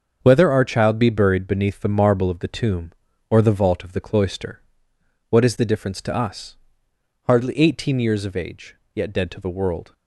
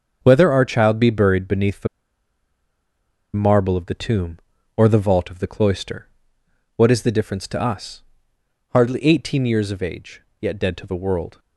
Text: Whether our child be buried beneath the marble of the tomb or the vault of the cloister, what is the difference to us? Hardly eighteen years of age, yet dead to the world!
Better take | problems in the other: first | starts louder than the rest; until 1.2 s; 6.5 dB; also in the first // pauses between "the" and "marble"; strong; at 1.8 s; 1.4 s long

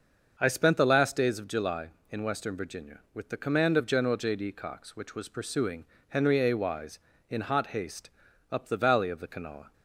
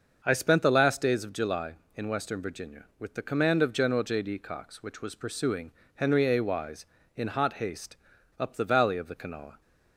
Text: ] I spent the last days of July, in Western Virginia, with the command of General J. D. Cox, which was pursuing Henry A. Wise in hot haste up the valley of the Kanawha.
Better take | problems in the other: neither | starts louder than the rest; the same in both // pauses between "pursuing" and "Henry"; slight; the same in both // pauses between "haste" and "up"; the same in both

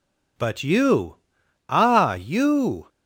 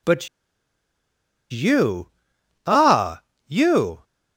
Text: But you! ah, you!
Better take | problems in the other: first | pauses between "But" and "you"; at 0.2 s; 1.2 s long

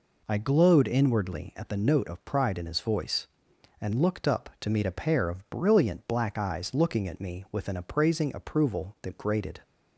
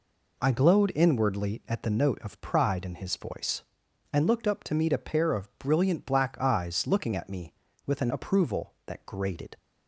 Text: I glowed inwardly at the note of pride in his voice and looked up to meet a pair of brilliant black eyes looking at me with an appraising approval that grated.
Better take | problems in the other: first | skips "appraising"; at 8.1 s

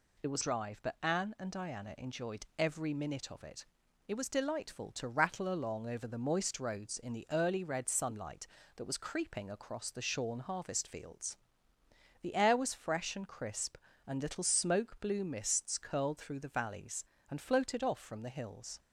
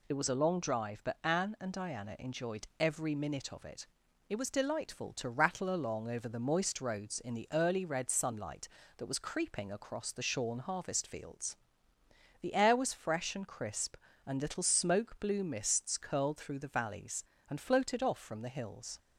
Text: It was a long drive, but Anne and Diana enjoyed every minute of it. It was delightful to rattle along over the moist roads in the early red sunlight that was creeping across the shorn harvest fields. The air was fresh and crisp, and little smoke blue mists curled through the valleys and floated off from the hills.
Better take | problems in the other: second | skips "a long"; at 0.4 s

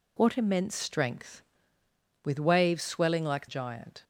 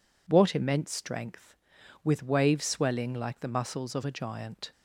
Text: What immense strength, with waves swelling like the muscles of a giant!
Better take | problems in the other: second | skips "the muscles of a"; at 3.4 s

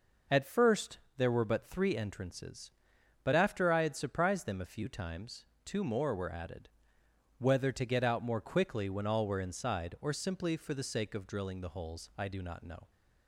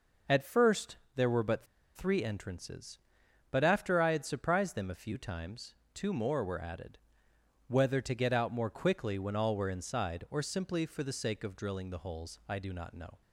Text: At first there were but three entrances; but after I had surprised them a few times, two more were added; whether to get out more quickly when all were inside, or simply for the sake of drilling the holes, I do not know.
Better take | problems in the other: first | pauses between "first" and "there"; slight; at 0.9 s; 0.20 s long; slight in the first // pauses between "but" and "three"; slight; at 1.6 s; 0.29 s long

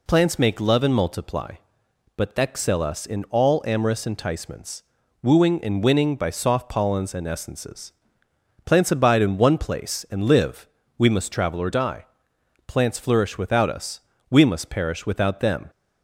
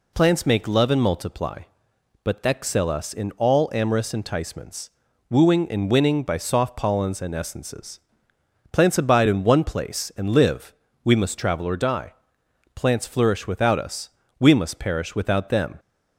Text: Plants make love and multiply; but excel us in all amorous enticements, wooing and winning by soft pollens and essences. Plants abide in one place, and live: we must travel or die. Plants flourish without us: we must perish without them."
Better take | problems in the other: neither | none

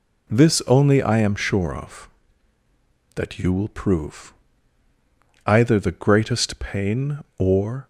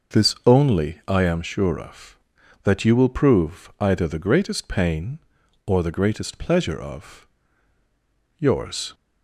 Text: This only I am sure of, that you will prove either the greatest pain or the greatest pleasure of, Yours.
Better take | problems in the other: second | pauses between "prove" and "either"; at 4.3 s; 1.1 s long // stops before "the greatest pleasure of Yours"; at 7.8 s

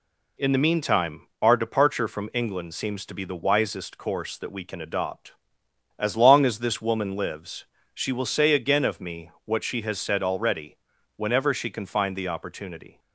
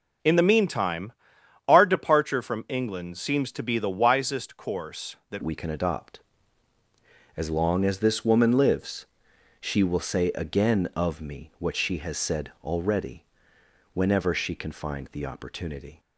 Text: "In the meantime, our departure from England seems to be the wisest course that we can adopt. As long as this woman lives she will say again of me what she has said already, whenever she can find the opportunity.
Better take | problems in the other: first | changes voice at "we"; from 5.4 s on; 10.5 s long // pauses between "lives" and "she"; noticeable; at 9.0 s; 0.54 s long; slight in the first

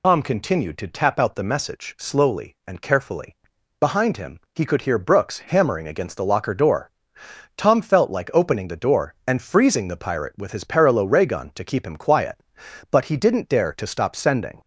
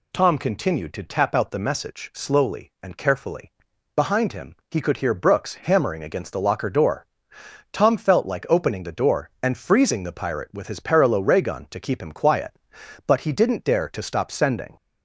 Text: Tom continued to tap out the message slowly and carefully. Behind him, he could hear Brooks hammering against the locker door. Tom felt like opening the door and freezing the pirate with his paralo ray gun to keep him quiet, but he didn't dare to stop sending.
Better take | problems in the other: second | loses the start of "Tom"; at 0.0 s; 65 ms

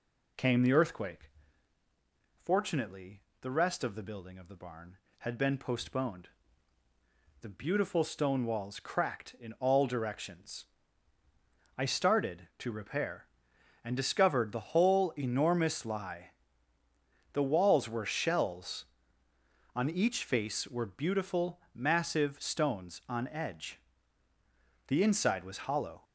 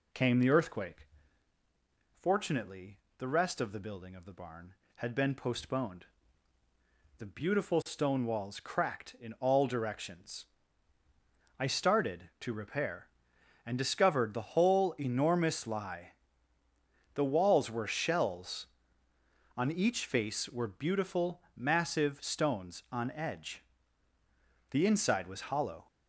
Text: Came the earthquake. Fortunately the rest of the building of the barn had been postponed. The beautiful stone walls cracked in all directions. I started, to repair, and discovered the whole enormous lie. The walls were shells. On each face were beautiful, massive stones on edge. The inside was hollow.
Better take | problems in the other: neither | pauses between "Fortunately" and "the"; slight; the same in both

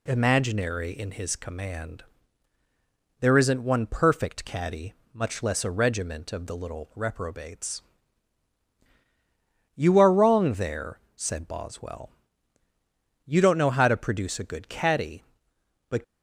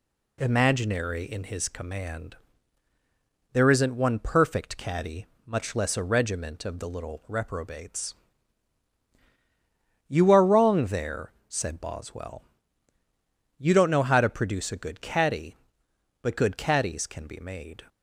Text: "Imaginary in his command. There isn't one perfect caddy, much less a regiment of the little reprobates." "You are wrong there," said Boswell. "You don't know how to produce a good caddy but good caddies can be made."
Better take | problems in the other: second | stops before "good caddies can be made"; at 16.0 s

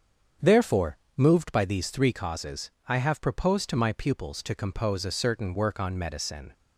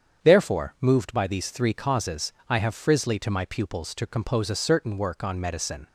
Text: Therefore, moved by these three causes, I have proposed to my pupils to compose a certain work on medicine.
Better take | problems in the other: first | starts louder than the rest; strong; until 1.3 s; 8 dB; strong in the first // says "frizzly" for "proposed"; at 2.7 s

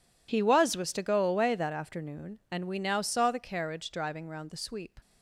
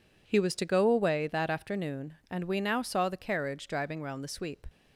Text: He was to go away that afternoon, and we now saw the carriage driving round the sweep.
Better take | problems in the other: second | says "was" twice; at 0.7 s

